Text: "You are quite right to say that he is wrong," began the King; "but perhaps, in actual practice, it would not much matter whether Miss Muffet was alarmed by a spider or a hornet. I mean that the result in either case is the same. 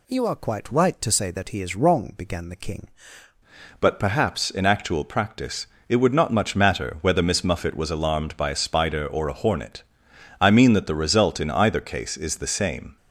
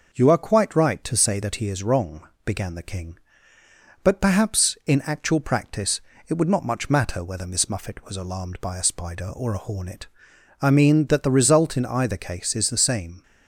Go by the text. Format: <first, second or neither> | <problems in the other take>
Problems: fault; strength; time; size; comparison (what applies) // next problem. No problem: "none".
second | changes voice at "but"; from 3.7 s on; 9.2 s long